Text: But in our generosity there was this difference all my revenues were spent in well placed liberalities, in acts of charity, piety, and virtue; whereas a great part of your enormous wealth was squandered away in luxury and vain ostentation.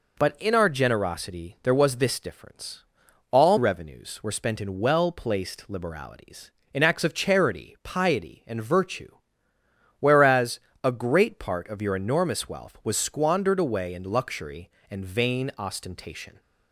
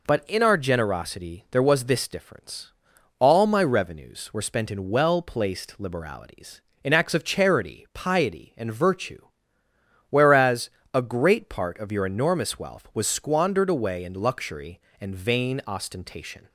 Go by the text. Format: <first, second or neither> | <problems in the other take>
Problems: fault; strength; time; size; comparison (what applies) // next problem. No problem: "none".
second | pauses between "difference" and "all"; noticeable; at 2.8 s; 0.46 s long; noticeable in the second // skips "my"; at 3.5 s // pauses between "whereas" and "a"; slight; at 10.5 s; 0.24 s long; slight in the second